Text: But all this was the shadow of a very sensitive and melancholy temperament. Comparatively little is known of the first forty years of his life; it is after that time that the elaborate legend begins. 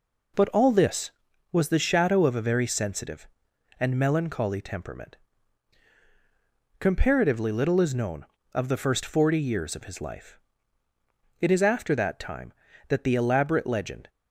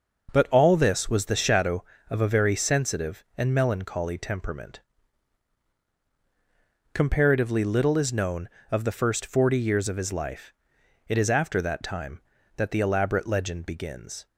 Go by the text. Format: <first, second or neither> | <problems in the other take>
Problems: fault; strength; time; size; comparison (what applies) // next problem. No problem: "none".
second | stops before "begins"; at 14.0 s